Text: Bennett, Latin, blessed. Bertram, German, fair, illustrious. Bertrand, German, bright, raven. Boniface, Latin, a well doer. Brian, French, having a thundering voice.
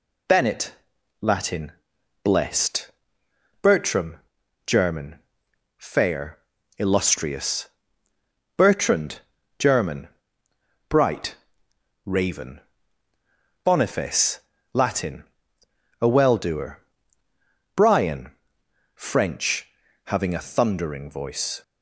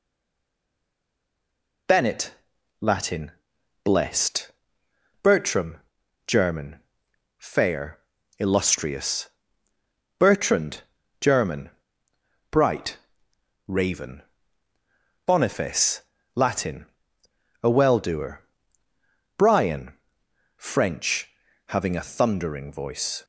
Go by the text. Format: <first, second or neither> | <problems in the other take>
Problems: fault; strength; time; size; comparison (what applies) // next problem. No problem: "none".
first | stays silent before the first word; noticeable; until 1.8 s; 1.8 s long